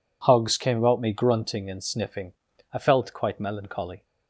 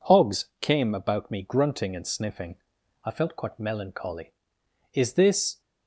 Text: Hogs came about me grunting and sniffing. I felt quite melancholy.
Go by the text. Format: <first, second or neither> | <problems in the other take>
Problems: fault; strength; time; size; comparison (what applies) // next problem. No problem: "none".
first | goes on to say "Is this"; noticeable; from 4.9 s on; 0.66 s long